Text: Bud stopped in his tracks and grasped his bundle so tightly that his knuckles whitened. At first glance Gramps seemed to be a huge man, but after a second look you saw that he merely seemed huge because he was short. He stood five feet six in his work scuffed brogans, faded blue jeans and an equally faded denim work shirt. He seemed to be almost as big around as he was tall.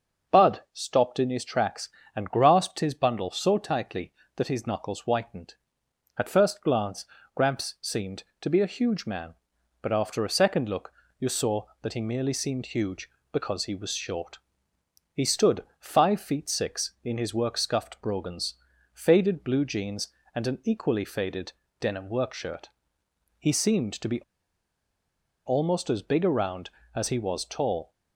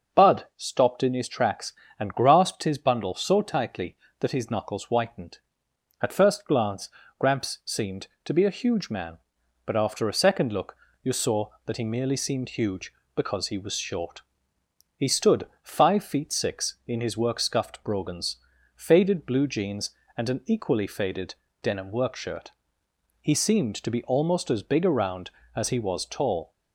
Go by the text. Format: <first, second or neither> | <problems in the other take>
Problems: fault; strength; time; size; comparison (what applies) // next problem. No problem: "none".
second | starts louder than the rest; noticeable; until 1.4 s; 6 dB; noticeable in the second // pauses between "glance" and "Gramps"; slight; at 7.0 s; 0.30 s long; slight in the second // pauses between "look" and "you"; slight; at 10.9 s; 0.28 s long; slight in the second // pauses between "stood" and "five"; slight; at 15.6 s; 0.16 s long; slight in the second // pauses between "faded" and "denim"; slight; at 21.5 s; 0.28 s long; slight in the second // pauses between "be" and "almost"; strong; at 24.2 s; 1.2 s long